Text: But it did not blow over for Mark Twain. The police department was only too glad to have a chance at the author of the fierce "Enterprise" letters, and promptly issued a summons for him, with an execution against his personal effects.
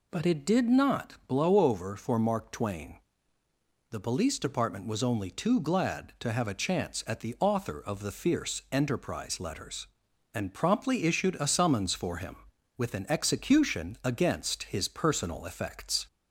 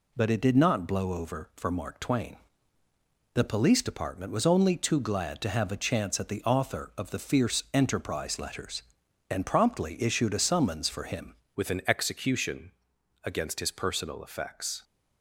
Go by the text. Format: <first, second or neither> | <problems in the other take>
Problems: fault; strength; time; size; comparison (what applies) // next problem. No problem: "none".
first | changes voice at "with"; from 11.5 s on; 3.3 s long // pauses between "execution" and "against"; noticeable; at 12.7 s; 0.52 s long